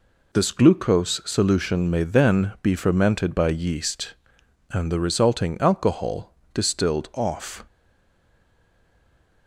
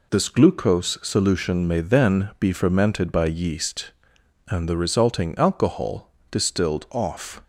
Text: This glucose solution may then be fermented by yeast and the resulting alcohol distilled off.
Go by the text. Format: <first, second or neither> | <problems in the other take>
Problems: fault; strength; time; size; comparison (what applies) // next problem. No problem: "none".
second | pauses between "alcohol" and "distilled"; slight; at 6.3 s; 0.22 s long; slight in the second // stays silent after the last word; noticeable; from 7.6 s on; 1.8 s long